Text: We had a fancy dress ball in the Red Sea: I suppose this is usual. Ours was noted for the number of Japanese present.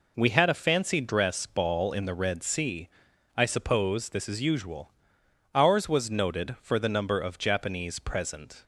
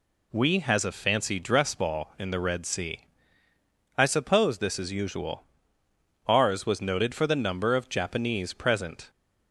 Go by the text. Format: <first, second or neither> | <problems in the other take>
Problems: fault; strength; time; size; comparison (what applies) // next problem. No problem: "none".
first | says "has" for "had"; at 0.5 s